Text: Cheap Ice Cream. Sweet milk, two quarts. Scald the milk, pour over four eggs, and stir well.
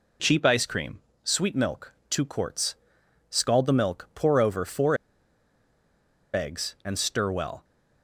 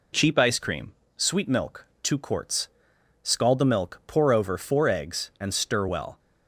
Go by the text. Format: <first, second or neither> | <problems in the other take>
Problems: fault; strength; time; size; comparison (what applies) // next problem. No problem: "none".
second | pauses between "four" and "eggs"; strong; at 4.9 s; 1.3 s long